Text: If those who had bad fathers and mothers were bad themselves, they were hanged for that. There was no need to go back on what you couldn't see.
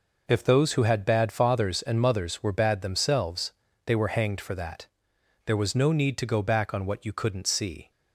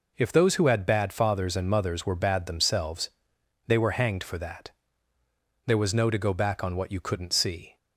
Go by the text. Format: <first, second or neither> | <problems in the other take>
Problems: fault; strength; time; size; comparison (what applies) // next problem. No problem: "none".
first | skips "need"; at 6.1 s